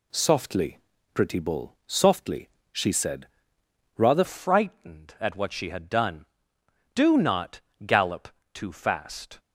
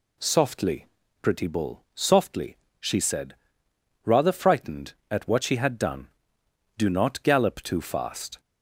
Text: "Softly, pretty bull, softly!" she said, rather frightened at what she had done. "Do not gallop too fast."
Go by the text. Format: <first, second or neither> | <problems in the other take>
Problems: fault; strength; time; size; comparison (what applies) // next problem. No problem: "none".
second | changes voice at "frightened"; from 4.2 s on; 5.1 s long // pauses between "not" and "gallop"; slight; at 7.5 s; 0.26 s long // pauses between "gallop" and "too"; slight; at 8.2 s; 0.24 s long